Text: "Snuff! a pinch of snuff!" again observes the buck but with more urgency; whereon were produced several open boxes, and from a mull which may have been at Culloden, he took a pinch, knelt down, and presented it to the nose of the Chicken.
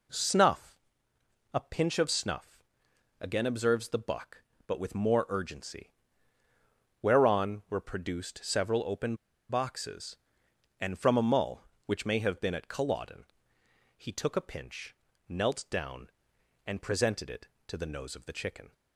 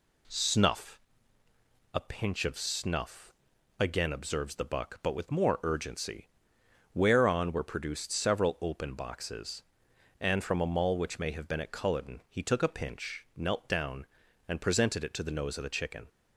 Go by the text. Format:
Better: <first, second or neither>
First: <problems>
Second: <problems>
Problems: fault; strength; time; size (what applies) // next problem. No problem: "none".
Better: second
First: pauses between "open" and "boxes"; slight; at 9.1 s; 0.34 s long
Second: none